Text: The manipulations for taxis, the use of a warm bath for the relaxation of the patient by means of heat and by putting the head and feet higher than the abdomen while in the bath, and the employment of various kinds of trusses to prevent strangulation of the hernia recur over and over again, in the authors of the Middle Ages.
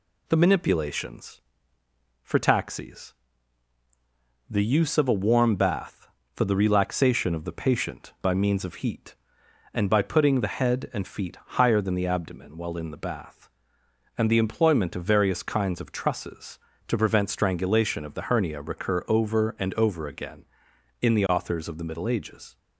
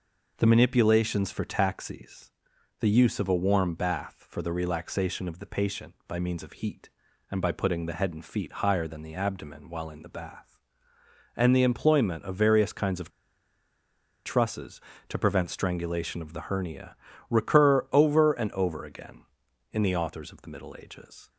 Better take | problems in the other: first | pauses between "of" and "trusses"; at 13.1 s; 1.1 s long // pauses between "hernia" and "recur"; slight; at 16.9 s; 0.34 s long

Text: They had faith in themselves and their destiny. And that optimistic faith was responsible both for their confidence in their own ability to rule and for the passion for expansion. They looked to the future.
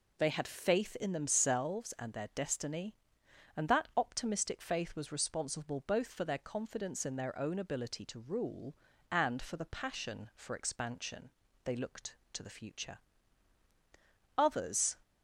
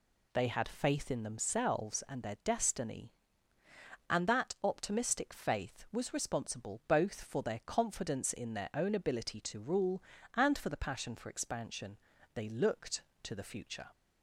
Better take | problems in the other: second | goes on to say "Others"; from 14.3 s on; 0.60 s long

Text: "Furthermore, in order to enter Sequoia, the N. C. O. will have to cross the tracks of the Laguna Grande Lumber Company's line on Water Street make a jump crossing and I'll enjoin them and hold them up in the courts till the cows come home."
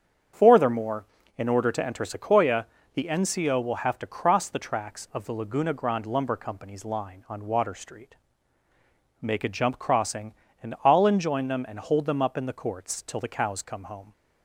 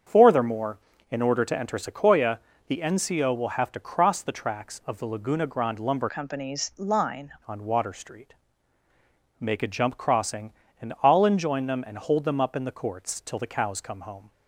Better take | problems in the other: first | starts louder than the rest; strong; until 1.4 s; 7.5 dB; strong in the first // changes voice from "Company's" to "line"; from 6.0 to 7.3 s; 1.3 s long // pauses between "Street" and "make"; at 8.3 s; 1.0 s long; also in the first

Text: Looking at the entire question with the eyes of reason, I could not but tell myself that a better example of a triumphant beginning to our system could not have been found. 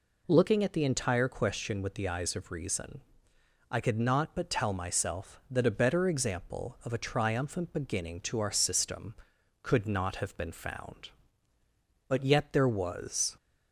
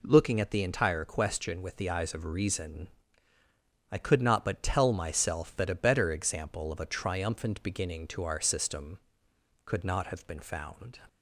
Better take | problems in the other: second | goes on to say "But yet there was"; noticeable; from 12.0 s on; 1.2 s long

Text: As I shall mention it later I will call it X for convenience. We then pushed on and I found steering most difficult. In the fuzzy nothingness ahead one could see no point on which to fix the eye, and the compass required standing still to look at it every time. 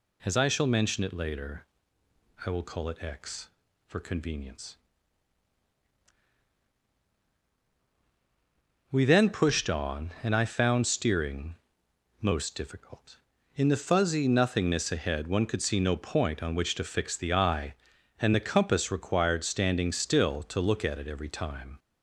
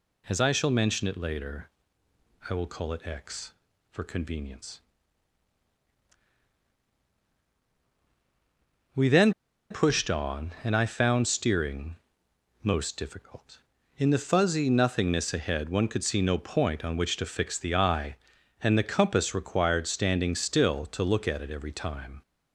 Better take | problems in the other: first | pauses between "later" and "I"; noticeable; at 1.6 s; 0.80 s long; noticeable in the first // pauses between "then" and "pushed"; at 9.3 s; 0.37 s long // pauses between "steering" and "most"; noticeable; at 11.9 s; 0.66 s long; noticeable in the first

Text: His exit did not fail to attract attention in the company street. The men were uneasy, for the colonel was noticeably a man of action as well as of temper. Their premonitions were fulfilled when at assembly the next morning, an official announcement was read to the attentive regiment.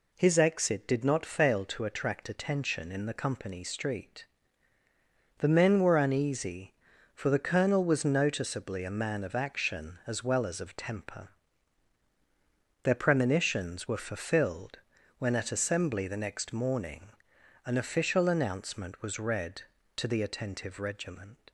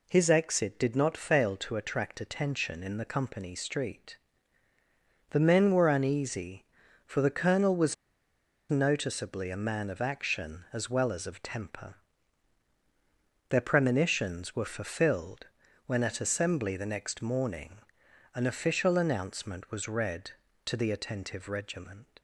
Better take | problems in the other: first | pauses between "was" and "noticeably"; noticeable; at 7.9 s; 0.75 s long // pauses between "fulfilled" and "when"; at 15.4 s; 0.40 s long; also in the first

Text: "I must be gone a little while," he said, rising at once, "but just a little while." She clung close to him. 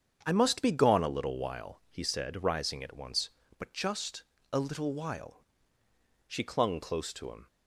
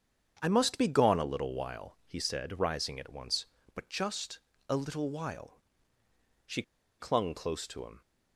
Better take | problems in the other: first | starts louder than the rest; strong; until 1.4 s; 7.5 dB; strong in the first // pauses between "just" and "a"; slight; at 4.3 s; 0.32 s long; slight in the first // pauses between "She" and "clung"; at 6.6 s; 0.38 s long

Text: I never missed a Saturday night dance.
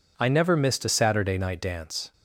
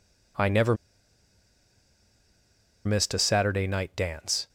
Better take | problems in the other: first | pauses between "never" and "missed"; strong; at 0.7 s; 2.1 s long

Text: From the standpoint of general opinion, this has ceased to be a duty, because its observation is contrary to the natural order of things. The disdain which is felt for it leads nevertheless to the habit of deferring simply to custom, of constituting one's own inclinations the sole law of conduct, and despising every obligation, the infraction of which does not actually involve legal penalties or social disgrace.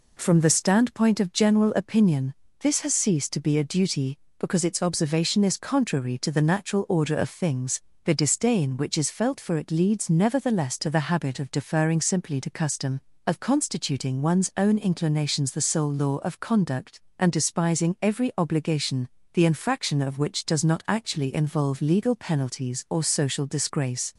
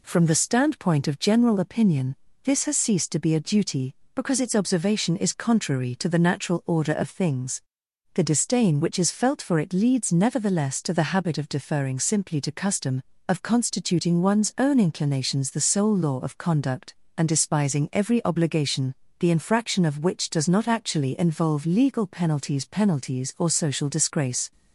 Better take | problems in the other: first | says "penalties" twice; at 22.6 s

